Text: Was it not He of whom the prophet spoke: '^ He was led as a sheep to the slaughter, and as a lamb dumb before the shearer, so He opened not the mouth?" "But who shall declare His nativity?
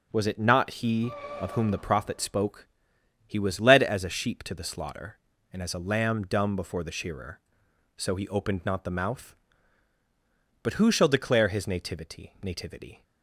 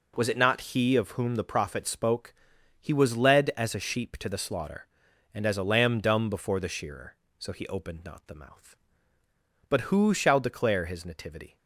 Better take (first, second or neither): second